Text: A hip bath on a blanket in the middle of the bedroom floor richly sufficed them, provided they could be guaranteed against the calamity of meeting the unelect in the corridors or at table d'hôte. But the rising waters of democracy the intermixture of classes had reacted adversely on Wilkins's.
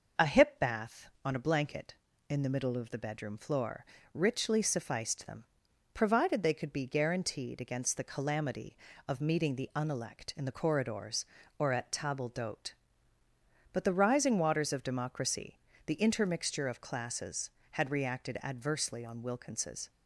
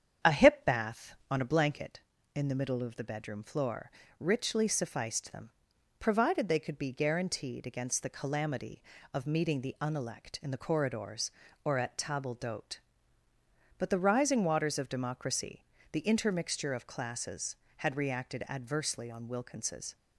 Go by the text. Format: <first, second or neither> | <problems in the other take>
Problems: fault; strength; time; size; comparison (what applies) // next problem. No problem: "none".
first | starts louder than the rest; strong; until 1.8 s; 8.5 dB // pauses between "floor" and "richly"; slight; at 3.8 s; 0.30 s long; slight in the first // pauses between "democracy" and "the"; slight; at 15.6 s; 0.26 s long; slight in the first